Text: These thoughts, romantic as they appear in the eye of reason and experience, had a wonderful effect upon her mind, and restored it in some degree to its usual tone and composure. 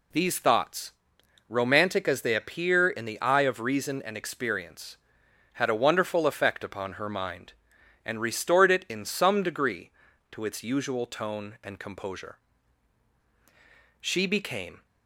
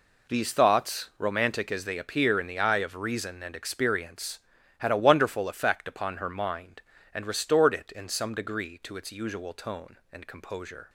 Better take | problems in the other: second | goes on to say "She became"; noticeable; from 14.0 s on; 0.84 s long

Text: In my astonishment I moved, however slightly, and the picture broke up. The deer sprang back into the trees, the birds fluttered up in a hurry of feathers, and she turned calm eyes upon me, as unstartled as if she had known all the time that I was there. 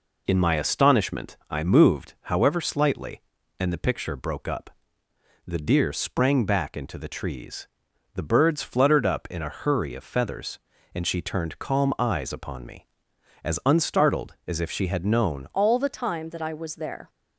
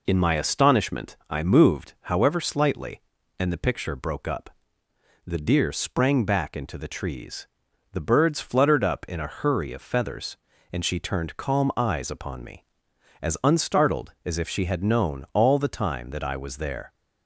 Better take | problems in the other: second | pauses between "astonishment" and "I"; slight; at 1.3 s; 0.16 s long; slight in the second // changes voice at "all"; from 15.5 s on; 1.5 s long

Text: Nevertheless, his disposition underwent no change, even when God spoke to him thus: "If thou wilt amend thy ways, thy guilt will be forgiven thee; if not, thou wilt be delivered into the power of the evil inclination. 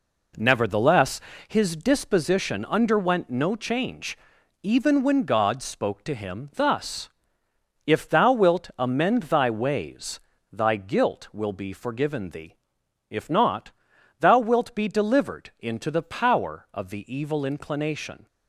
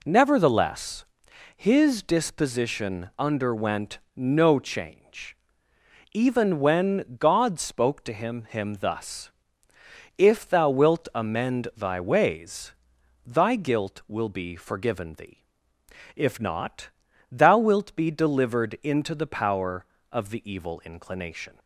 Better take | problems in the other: first | pauses between "underwent" and "no"; slight; at 3.9 s; 0.18 s long // says "him" twice; at 8.4 s

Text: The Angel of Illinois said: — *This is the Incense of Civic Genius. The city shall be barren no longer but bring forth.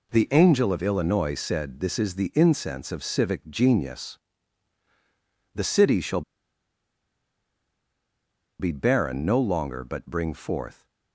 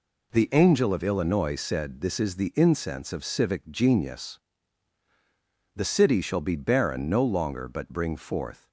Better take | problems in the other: second | pauses between "shall" and "be"; strong; at 6.2 s; 2.3 s long

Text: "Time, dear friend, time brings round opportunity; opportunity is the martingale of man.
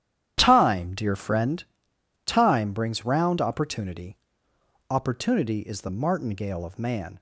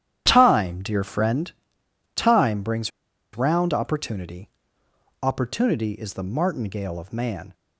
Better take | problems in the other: first | starts louder than the rest; strong; until 1.2 s; 10.5 dB; strong in the first // pauses between "brings" and "round"; at 2.9 s; 0.45 s long

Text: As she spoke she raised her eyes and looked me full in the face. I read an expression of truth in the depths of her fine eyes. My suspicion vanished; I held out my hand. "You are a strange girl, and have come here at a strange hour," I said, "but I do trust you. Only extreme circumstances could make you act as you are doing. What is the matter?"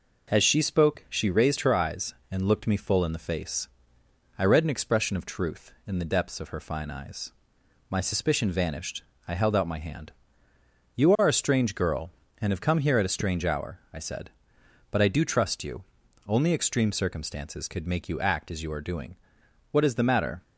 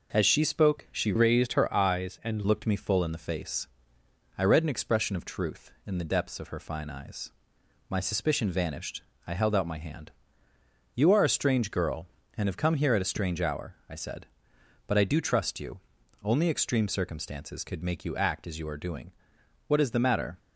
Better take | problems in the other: first | changes voice from "raised" to "and"; from 1.1 to 2.4 s; 1.3 s long

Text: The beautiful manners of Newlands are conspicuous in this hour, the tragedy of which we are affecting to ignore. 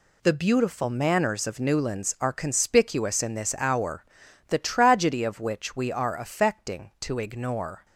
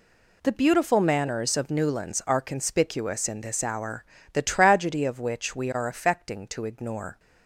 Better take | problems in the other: neither | none

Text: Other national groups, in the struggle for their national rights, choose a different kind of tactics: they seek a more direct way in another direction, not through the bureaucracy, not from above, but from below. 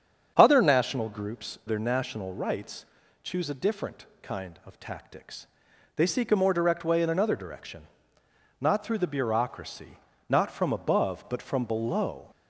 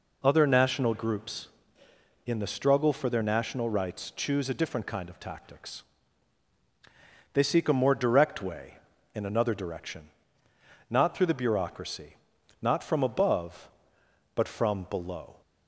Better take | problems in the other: second | starts louder than the rest; strong; until 1.3 s; 7.5 dB // skips "in the struggle for"; at 1.6 s // pauses between "different" and "kind"; slight; at 4.0 s; 0.16 s long

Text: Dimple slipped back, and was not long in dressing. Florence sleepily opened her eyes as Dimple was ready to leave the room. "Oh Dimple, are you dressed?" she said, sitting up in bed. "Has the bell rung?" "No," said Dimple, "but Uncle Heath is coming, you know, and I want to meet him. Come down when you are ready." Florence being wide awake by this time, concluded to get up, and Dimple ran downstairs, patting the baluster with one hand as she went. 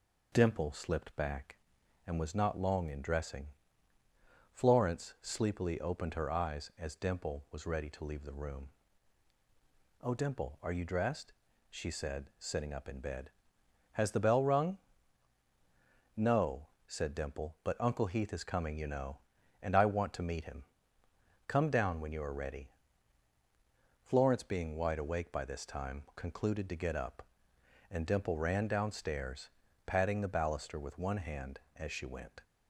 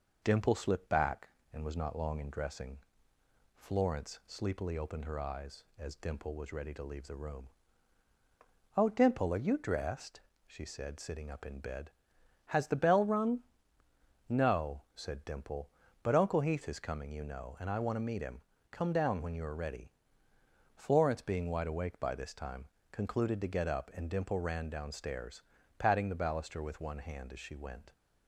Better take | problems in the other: neither | none

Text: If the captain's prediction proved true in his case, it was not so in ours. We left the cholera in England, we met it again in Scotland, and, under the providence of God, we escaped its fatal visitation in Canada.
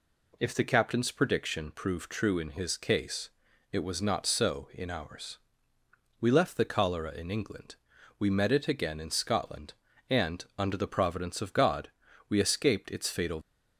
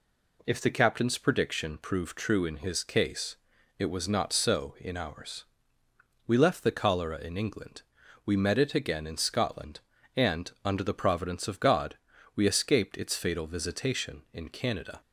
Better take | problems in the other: second | stops before "visitation in Canada"; at 13.4 s

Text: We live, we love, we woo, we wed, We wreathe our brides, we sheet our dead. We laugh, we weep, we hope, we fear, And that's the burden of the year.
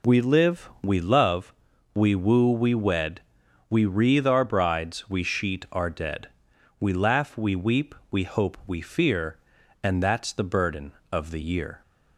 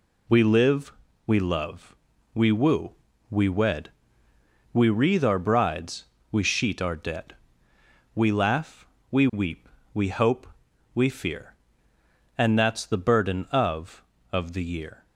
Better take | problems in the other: first | says "of" twice; at 14.3 s

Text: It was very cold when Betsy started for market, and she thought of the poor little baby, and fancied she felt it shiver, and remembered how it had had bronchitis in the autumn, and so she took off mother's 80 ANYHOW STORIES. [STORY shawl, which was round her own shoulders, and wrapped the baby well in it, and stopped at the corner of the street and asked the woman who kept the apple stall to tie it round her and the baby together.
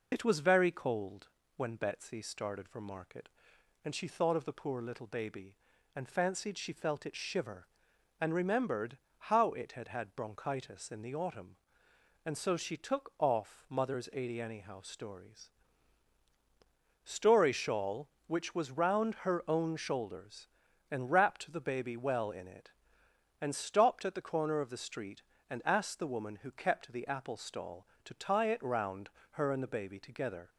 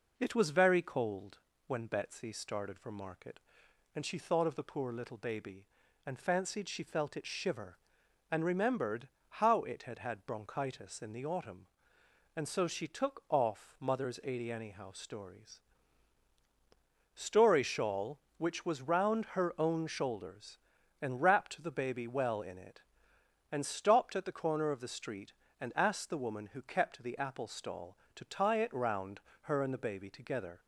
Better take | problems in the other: second | loses the start of "It"; at 0.1 s; 50 ms // pauses between "cold" and "when"; slight; at 1.2 s; 0.28 s long; slight in the second // pauses between "remembered" and "how"; slight; at 8.9 s; 0.22 s long; slight in the second // pauses between "round" and "her"; slight; at 29.0 s; 0.22 s long; slight in the second

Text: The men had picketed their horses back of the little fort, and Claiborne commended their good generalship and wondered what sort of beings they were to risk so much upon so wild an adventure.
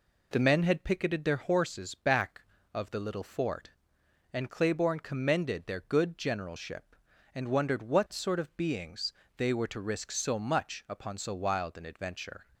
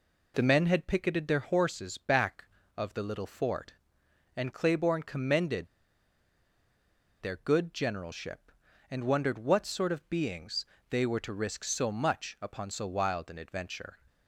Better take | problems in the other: first | pauses between "commended" and "their"; strong; at 5.6 s; 1.5 s long // pauses between "beings" and "they"; slight; at 10.6 s; 0.24 s long; slight in the first

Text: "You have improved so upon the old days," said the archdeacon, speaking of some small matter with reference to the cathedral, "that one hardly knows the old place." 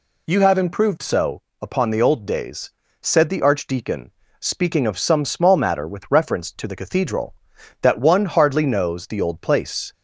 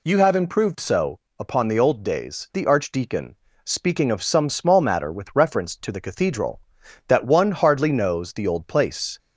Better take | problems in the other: first | pauses between "so" and "upon"; slight; at 1.1 s; 0.20 s long; slight in the first // skips "said"; at 2.5 s

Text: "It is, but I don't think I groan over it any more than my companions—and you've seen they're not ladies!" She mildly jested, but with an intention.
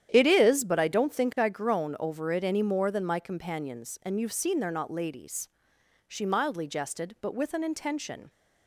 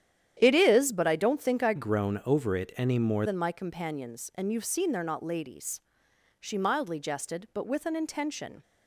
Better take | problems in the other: first | starts louder than the rest; strong; until 1.4 s; 10 dB; strong in the first // changes voice from "groan" to "more"; from 1.7 to 3.2 s; 1.5 s long

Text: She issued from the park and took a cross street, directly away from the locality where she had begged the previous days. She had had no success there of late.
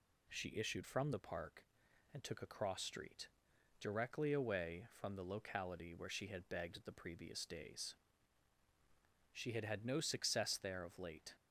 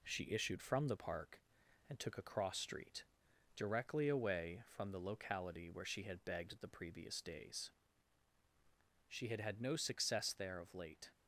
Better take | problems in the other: first | gets quieter; slight; throughout; 2.5 dB

